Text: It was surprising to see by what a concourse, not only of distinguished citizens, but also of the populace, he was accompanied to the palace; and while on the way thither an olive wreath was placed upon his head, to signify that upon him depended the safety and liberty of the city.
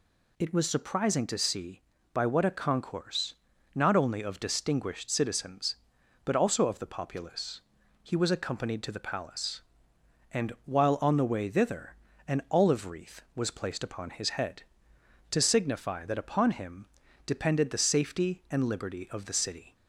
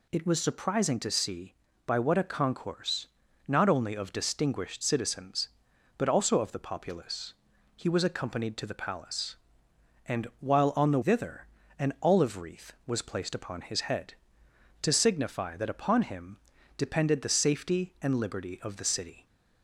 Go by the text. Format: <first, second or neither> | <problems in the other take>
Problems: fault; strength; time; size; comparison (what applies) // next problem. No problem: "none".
first | skips "way"; at 11.0 s // pauses between "thither" and "an"; slight; at 11.4 s; 0.32 s long; slight in the first // pauses between "him" and "depended"; at 16.3 s; 0.40 s long; also in the first